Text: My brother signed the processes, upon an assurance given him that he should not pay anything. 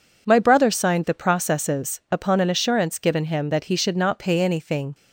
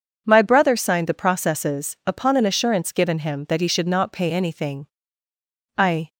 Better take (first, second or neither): first